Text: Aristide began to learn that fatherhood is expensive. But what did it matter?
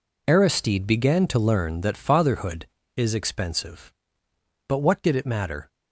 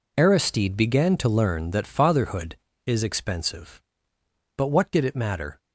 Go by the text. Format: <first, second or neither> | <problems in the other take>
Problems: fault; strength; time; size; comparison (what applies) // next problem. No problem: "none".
neither | none